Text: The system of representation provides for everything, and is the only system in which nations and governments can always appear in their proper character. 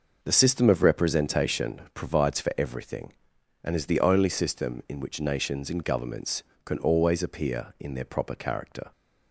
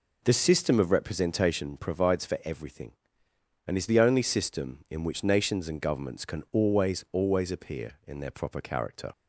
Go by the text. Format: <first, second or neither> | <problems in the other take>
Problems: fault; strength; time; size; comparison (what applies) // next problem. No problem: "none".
first | says "always" twice; at 7.1 s